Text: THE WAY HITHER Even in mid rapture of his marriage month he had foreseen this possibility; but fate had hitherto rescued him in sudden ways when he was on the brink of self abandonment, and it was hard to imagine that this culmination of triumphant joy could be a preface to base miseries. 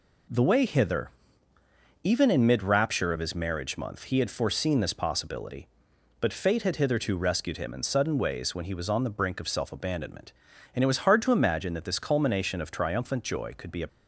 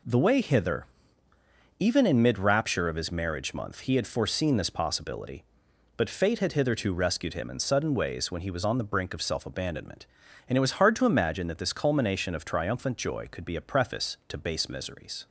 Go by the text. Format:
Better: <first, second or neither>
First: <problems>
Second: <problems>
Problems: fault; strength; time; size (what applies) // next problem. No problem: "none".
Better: second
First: pauses between "HITHER" and "Even"; noticeable; at 1.0 s; 0.94 s long // stops before "preface to base miseries"; at 13.8 s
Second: pauses between "HITHER" and "Even"; noticeable; at 0.8 s; 0.94 s long